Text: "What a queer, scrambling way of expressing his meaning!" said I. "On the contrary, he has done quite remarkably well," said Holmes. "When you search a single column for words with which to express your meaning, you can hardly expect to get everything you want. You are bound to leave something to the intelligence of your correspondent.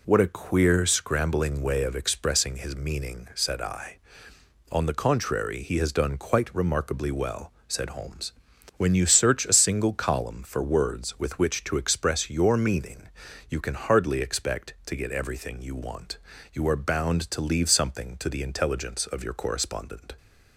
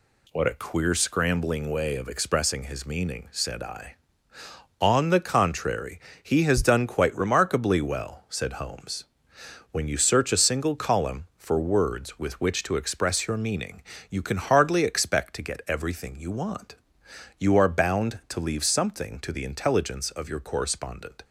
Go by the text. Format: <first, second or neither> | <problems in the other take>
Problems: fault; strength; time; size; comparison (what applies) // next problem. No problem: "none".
neither | none